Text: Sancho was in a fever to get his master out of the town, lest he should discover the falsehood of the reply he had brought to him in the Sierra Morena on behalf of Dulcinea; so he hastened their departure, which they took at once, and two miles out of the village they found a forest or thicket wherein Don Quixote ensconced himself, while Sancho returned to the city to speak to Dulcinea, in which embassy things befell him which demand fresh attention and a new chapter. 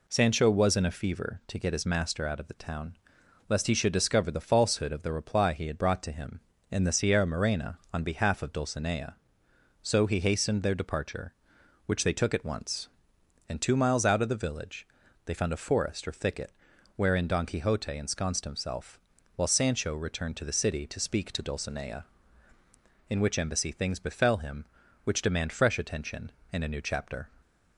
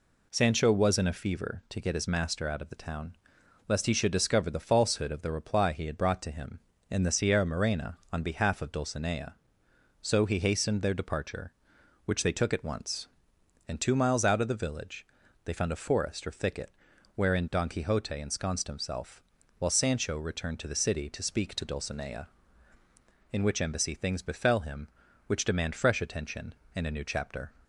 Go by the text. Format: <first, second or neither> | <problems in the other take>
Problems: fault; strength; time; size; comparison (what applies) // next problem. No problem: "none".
neither | pauses between "village" and "they"; the same in both // pauses between "thicket" and "wherein"; the same in both